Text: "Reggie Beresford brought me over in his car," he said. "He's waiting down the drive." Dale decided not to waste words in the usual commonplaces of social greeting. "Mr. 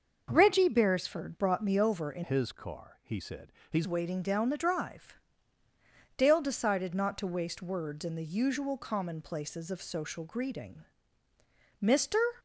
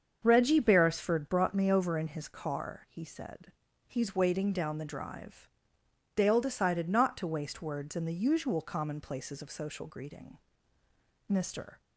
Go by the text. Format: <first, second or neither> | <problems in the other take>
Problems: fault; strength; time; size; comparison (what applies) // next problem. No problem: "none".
second | starts louder than the rest; noticeable; until 1.3 s; 6 dB; also in the second // changes voice from "his" to "He's"; from 2.2 to 3.8 s; 1.6 s long